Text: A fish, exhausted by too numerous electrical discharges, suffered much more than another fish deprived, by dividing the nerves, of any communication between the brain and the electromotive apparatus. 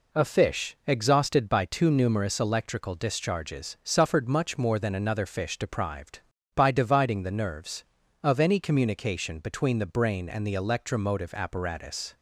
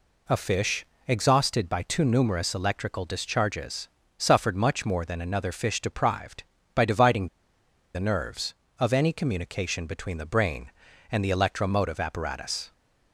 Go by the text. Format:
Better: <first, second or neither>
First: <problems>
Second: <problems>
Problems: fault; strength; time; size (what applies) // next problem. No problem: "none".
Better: first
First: none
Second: pauses between "dividing" and "the"; noticeable; at 7.2 s; 0.66 s long